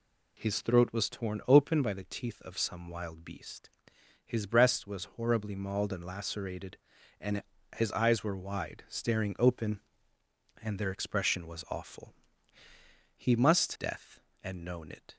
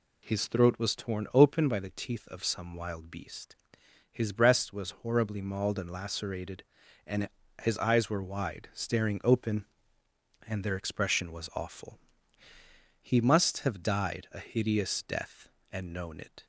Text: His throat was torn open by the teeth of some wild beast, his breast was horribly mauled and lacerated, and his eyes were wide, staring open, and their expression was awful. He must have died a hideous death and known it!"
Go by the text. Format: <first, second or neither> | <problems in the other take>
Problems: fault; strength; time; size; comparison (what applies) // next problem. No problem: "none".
second | pauses between "and" and "his"; slight; at 7.4 s; 0.34 s long; slight in the second // skips "have died a hideous"; at 13.7 s